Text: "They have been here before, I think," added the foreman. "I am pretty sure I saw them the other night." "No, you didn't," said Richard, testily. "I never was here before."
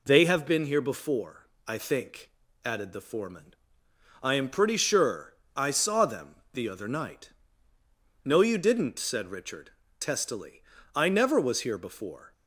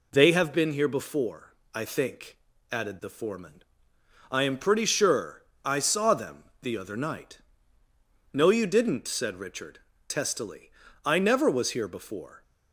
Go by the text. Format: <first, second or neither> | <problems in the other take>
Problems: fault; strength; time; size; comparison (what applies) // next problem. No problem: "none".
neither | pauses between "sure" and "I"; slight; the same in both // pauses between "them" and "the"; slight; the same in both